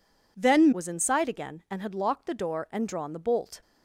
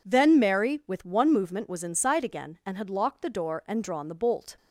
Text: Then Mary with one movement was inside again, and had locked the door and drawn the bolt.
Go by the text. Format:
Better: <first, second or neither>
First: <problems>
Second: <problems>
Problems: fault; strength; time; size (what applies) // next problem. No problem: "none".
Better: second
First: skips "Mary with one movement"; at 0.7 s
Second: none